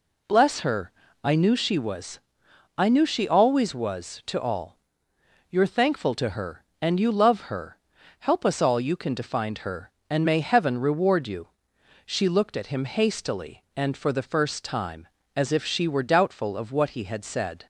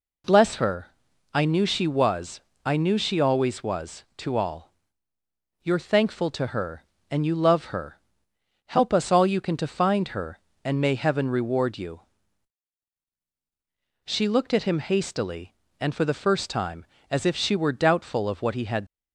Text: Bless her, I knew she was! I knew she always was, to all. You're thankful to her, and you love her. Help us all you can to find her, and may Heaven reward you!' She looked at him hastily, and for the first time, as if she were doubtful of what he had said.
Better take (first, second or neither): first